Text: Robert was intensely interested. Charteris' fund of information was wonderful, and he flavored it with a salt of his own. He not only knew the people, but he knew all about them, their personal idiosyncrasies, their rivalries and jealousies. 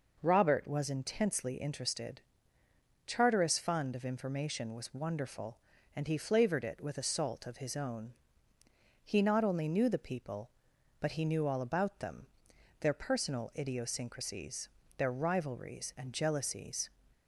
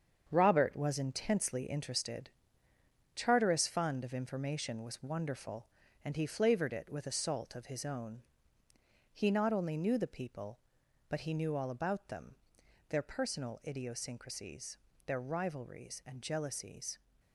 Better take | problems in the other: first | gets quieter; strong; throughout; 7.5 dB

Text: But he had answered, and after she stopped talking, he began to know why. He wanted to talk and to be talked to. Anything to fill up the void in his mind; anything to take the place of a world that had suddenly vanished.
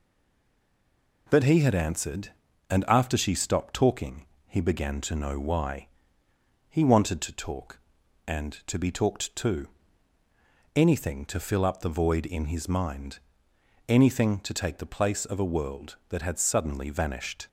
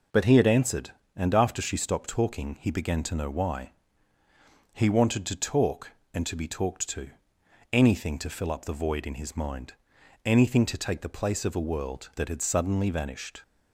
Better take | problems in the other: second | stays silent before the first word; noticeable; until 1.2 s; 1.2 s long

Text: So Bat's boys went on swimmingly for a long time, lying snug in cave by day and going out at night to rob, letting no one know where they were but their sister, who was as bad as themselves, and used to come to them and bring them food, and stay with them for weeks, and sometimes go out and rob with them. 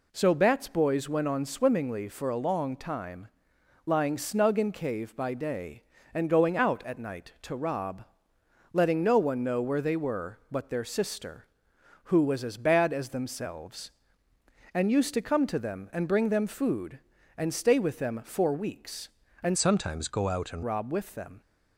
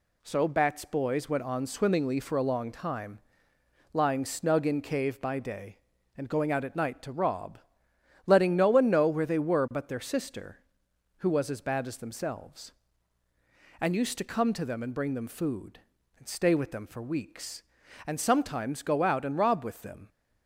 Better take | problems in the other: second | changes voice from "sometimes" to "and"; from 19.5 to 20.6 s; 1.1 s long

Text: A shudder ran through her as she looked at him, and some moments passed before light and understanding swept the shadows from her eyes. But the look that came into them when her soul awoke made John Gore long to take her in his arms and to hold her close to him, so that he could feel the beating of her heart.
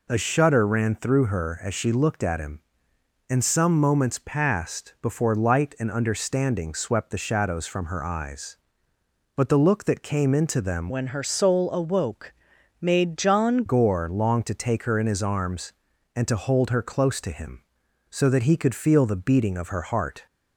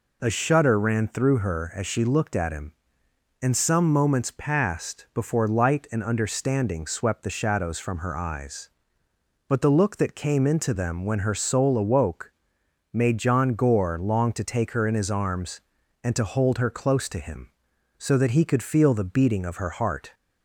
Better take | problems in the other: second | changes voice from "when" to "John"; from 10.8 to 13.6 s; 2.8 s long // pauses between "awoke" and "made"; noticeable; at 12.3 s; 0.48 s long; noticeable in the second

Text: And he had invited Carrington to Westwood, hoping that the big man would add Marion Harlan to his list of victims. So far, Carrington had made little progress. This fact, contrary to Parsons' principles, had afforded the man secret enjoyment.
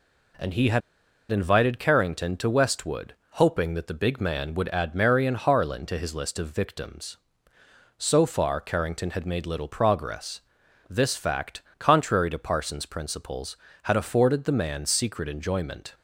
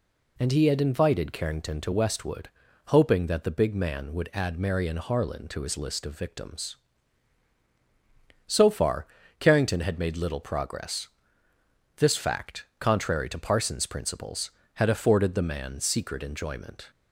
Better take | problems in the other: second | pauses between "had" and "invited"; noticeable; at 0.8 s; 0.51 s long

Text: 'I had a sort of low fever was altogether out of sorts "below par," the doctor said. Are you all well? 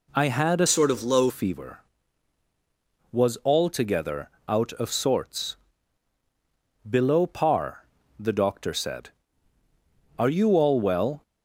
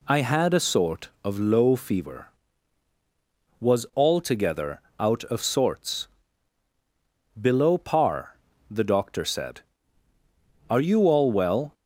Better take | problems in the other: second | changes voice from "sort" to "low"; from 0.6 to 1.3 s; 0.7 s long // pauses between "altogether" and "out"; slight; at 4.2 s; 0.20 s long; slight in the second // pauses between "sorts" and "below"; strong; at 5.5 s; 1.3 s long; strong in the second

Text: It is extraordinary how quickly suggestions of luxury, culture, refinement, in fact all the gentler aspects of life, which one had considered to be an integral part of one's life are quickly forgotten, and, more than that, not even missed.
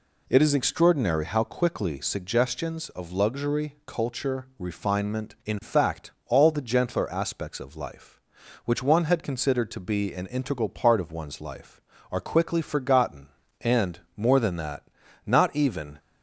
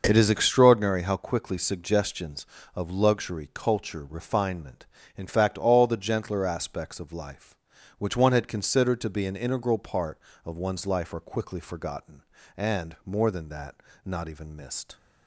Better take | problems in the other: second | pauses between "fact" and "all"; slight; at 6.1 s; 0.16 s long // stops before "missed"; at 15.9 s

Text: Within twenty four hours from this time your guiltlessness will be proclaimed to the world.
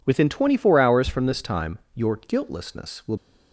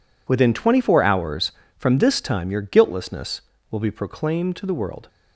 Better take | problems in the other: second | pauses between "time" and "your"; slight; at 1.7 s; 0.16 s long // stops before "be proclaimed to the world"; at 3.1 s

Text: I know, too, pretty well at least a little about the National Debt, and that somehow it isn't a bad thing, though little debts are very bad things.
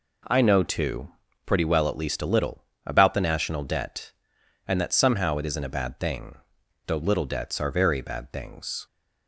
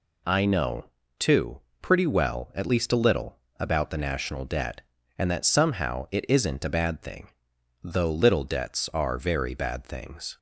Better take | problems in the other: neither | pauses between "little" and "about"; slight; the same in both

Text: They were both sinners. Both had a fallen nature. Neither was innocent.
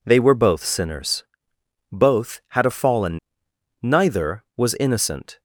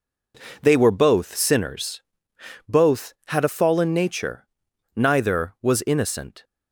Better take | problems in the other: second | skips "nature"; at 3.4 s

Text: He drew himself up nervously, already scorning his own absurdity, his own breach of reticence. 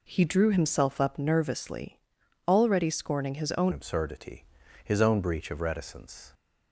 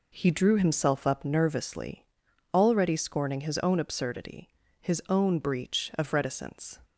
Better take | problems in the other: second | changes voice at "absurdity"; from 3.7 s on; 2.6 s long

